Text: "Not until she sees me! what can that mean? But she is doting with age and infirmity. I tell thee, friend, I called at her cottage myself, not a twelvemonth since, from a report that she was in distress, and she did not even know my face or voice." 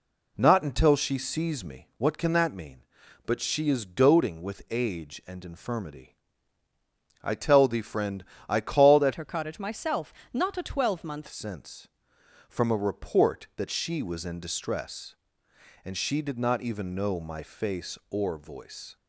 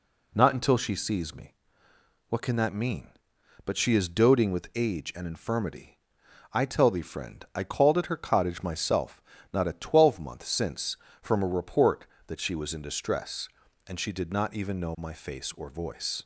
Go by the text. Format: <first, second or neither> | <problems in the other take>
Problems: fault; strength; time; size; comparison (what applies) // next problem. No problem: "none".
second | changes voice from "her" to "twelvemonth"; from 9.1 to 11.2 s; 2.1 s long